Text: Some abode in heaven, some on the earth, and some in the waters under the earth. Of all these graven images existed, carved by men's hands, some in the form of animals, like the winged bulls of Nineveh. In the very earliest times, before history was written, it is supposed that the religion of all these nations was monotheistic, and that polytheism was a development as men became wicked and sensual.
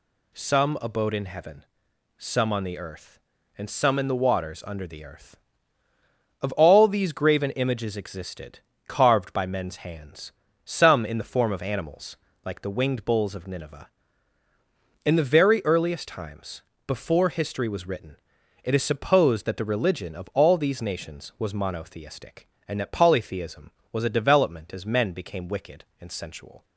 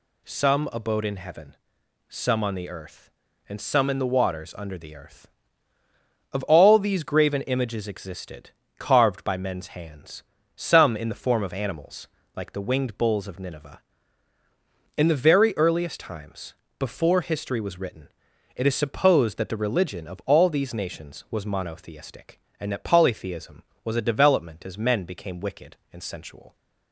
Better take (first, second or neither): neither